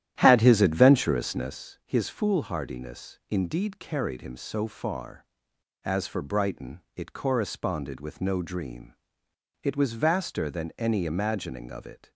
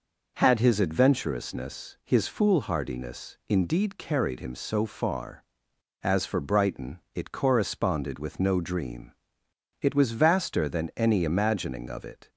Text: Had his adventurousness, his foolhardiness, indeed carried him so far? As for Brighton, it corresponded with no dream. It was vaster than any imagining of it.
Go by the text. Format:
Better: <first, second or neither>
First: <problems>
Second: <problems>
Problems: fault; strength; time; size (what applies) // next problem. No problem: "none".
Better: second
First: starts louder than the rest; strong; until 1.7 s; 11.5 dB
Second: none